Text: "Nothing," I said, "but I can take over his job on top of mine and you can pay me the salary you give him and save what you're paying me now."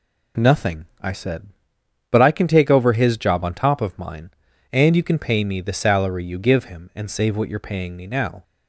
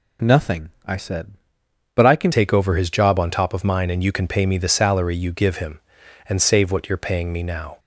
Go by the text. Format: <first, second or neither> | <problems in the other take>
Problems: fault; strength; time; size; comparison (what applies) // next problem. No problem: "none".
first | changes voice at "take"; from 2.3 s on; 5.4 s long